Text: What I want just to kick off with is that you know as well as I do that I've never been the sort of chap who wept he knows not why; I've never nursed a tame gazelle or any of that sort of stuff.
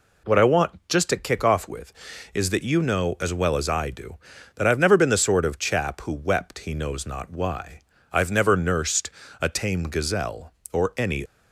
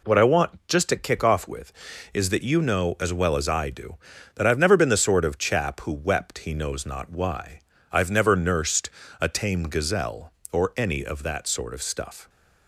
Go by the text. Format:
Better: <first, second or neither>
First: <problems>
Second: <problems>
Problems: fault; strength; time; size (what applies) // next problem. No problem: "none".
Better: second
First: pauses between "nursed" and "a"; slight; at 9.0 s; 0.32 s long // stops before "of that sort of stuff"; at 11.2 s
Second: pauses between "nursed" and "a"; slight; at 8.8 s; 0.32 s long